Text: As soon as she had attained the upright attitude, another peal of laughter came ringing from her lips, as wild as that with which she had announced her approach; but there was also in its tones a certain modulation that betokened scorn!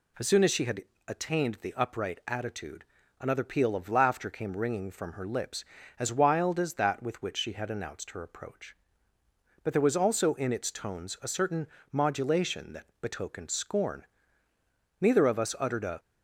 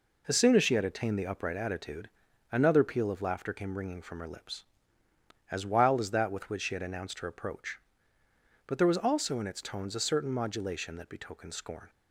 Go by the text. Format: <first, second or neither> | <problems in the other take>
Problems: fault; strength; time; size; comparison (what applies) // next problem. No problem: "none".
second | pauses between "had" and "attained"; slight; at 0.8 s; 0.24 s long // pauses between "certain" and "modulation"; slight; at 11.6 s; 0.24 s long // goes on to say "Neither of us uttered a"; noticeable; from 15.0 s on; 0.98 s long